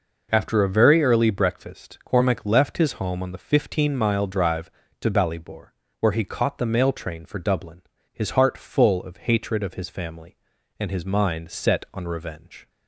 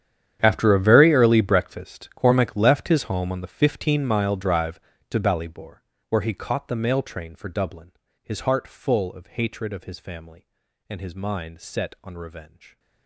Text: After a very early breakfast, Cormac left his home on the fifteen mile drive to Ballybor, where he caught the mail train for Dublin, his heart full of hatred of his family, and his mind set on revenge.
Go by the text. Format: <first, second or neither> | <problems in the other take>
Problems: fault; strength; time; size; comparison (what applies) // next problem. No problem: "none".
first | gets quieter; strong; throughout; 18 dB